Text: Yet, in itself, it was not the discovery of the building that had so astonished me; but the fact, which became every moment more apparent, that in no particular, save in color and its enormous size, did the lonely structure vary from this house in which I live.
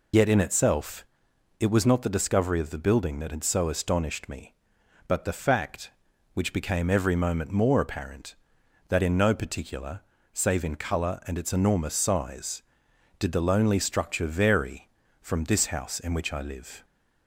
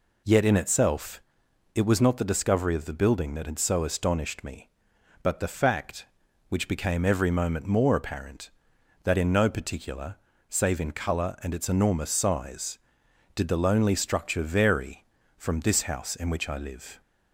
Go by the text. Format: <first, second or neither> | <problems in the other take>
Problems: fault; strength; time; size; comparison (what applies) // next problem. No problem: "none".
second | loses the start of "Yet"; at 0.1 s; 45 ms